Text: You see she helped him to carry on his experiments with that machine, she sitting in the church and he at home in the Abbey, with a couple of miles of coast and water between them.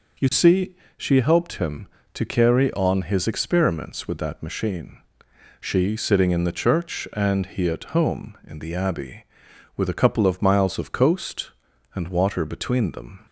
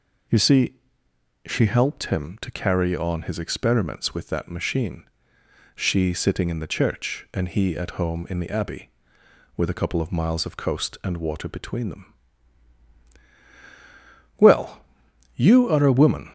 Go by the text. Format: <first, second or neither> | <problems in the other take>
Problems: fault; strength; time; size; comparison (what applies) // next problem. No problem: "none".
first | pauses between "see" and "she"; noticeable; at 0.7 s; 0.70 s long; slight in the first // goes on to say "Well you are a woman"; strong; from 14.3 s on; 1.9 s long